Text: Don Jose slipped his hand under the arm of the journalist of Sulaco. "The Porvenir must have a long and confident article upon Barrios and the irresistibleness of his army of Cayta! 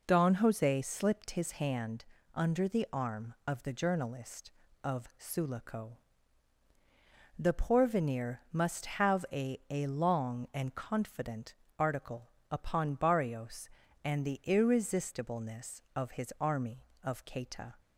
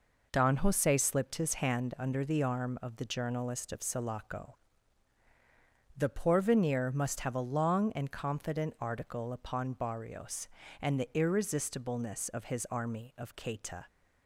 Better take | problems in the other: second | pauses between "hand" and "under"; slight; at 2.0 s; 0.32 s long // says "a" twice; at 9.6 s // pauses between "confident" and "article"; slight; at 11.5 s; 0.24 s long // pauses between "article" and "upon"; slight; at 12.3 s; 0.18 s long

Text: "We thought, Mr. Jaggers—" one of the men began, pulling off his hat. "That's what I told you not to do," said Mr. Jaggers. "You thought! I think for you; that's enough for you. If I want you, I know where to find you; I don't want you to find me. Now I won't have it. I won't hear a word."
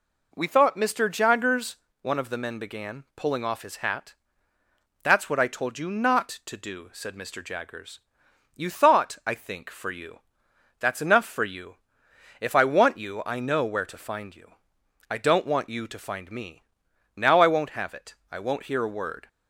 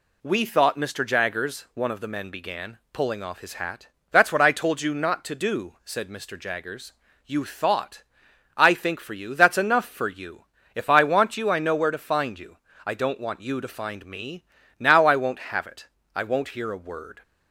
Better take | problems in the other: neither | none

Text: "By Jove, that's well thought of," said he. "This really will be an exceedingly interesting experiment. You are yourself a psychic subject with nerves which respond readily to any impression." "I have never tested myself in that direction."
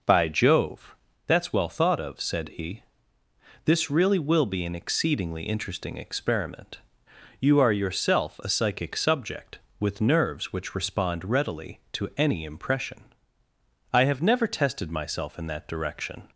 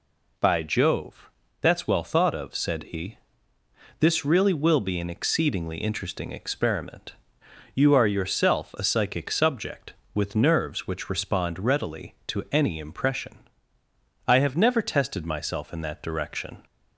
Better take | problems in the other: second | starts louder than the rest; noticeable; until 1.3 s; 5.5 dB

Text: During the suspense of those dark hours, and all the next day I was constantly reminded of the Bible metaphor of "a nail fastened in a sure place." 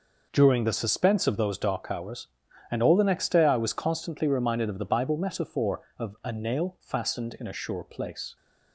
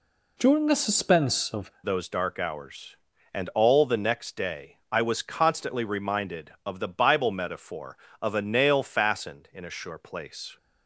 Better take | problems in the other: first | changes voice at "those"; from 1.8 s on; 8.7 s long

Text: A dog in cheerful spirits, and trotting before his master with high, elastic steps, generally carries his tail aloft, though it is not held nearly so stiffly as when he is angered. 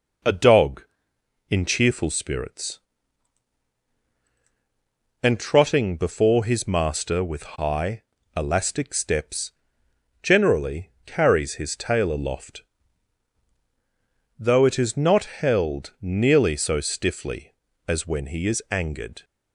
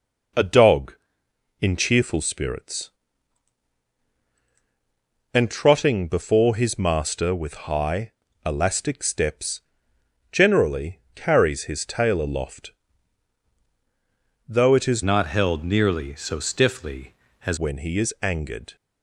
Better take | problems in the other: first | changes voice from "not" to "as"; from 15.0 to 17.5 s; 2.5 s long

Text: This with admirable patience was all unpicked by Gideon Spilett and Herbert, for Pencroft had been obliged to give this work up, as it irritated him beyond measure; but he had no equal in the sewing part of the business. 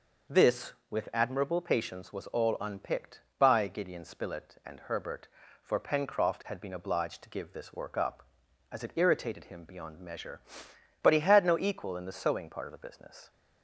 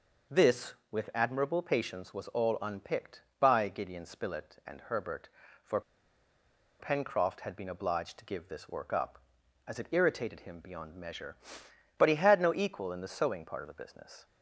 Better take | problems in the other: first | pauses between "for" and "Pencroft"; at 5.8 s; 0.99 s long

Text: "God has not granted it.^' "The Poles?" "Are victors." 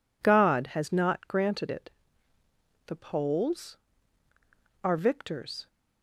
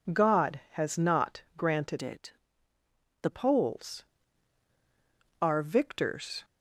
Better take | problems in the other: first | changes voice from "it" to "The"; from 2.0 to 3.2 s; 1.2 s long

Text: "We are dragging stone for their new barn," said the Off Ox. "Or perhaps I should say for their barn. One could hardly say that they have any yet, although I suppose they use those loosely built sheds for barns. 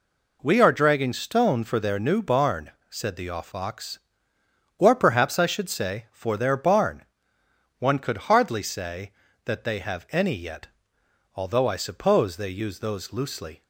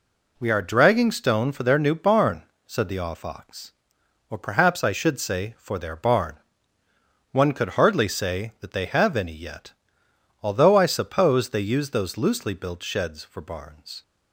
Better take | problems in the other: second | stops before "built sheds for barns"; at 13.6 s

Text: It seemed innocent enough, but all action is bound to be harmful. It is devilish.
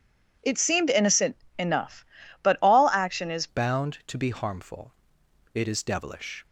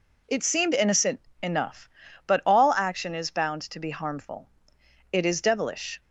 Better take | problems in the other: second | pauses between "innocent" and "enough"; slight; at 1.3 s; 0.24 s long; slight in the second // changes voice at "bound"; from 3.4 s on; 3.0 s long

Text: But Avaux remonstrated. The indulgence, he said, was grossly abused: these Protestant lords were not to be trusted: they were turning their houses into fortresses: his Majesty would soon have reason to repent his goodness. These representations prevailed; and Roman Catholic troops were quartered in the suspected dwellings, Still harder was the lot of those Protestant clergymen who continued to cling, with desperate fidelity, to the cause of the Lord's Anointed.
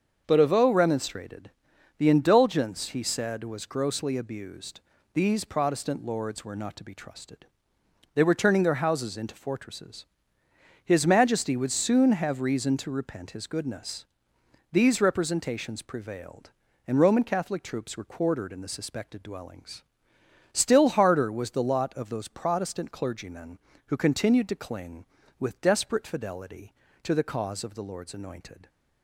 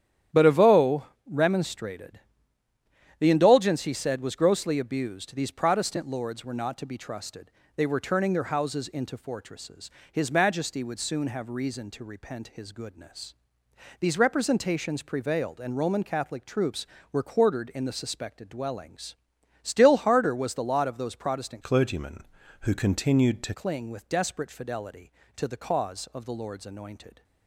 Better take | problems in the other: first | starts louder than the rest; strong; until 1.5 s; 10.5 dB; also in the first // pauses between "Avaux" and "remonstrated"; slight; at 1.0 s; 0.22 s long // changes voice from "clergymen" to "to"; from 21.6 to 23.5 s; 1.9 s long

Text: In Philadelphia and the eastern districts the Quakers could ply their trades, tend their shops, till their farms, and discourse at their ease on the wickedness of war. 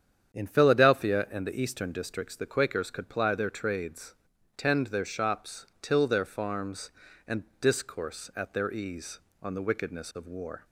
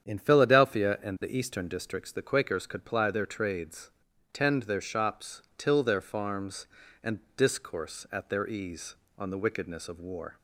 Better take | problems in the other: neither | starts louder than the rest; strong; the same in both // pauses between "and" and "discourse"; slight; the same in both

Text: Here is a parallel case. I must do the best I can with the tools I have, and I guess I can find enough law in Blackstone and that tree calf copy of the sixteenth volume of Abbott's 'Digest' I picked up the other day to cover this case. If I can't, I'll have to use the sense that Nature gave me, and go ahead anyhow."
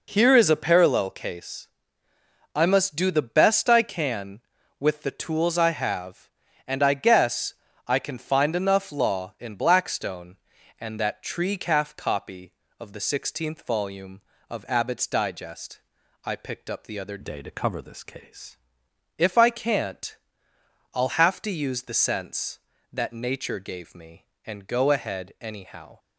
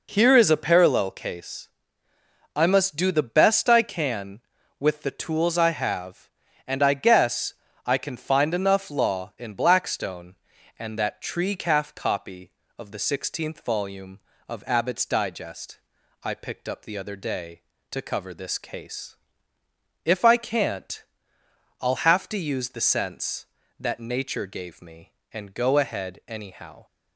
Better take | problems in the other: second | pauses between "guess" and "I"; slight; at 7.5 s; 0.34 s long; slight in the second // pauses between "Digest" and "I"; noticeable; at 15.7 s; 0.46 s long; noticeable in the second // changes voice from "day" to "case"; from 17.2 to 18.5 s; 1.3 s long

